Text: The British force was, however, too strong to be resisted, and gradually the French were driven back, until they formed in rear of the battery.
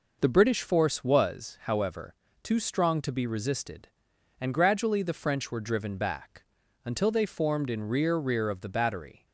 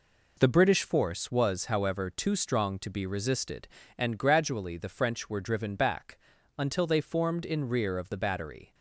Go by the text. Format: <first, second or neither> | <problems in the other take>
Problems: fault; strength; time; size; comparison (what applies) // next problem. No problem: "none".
second | says "rear" twice; at 8.1 s